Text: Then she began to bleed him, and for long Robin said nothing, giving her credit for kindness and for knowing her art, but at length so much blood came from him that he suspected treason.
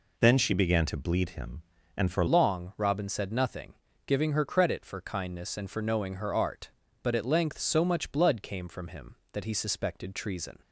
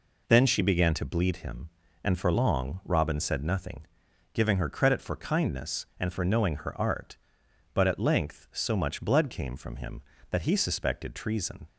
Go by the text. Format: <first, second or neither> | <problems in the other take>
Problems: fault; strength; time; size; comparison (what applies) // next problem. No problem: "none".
second | changes voice at "long"; from 2.2 s on; 8.3 s long